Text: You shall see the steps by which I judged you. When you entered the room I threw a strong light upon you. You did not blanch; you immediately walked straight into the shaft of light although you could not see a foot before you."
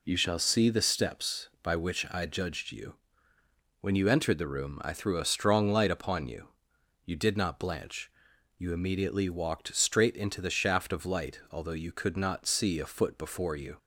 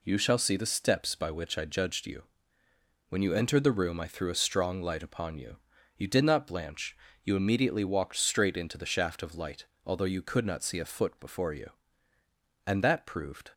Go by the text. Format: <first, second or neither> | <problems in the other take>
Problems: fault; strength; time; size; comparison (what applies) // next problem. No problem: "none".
first | pauses between "light" and "although"; slight; at 9.6 s; 0.20 s long // goes on to say "And that proved"; noticeable; from 12.6 s on; 0.86 s long